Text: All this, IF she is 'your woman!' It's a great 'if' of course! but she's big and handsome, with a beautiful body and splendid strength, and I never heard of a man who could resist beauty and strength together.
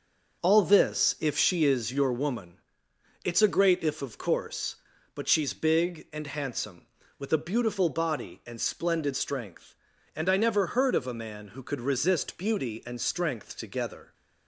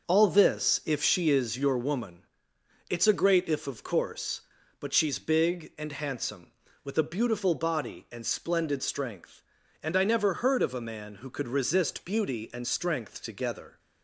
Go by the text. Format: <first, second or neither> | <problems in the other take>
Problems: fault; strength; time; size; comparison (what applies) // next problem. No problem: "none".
neither | none